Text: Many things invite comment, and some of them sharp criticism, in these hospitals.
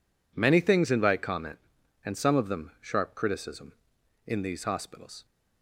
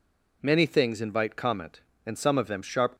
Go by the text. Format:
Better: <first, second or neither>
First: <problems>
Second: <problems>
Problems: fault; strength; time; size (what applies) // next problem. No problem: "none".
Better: first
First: none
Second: stops before "criticism in these hospitals"; at 2.9 s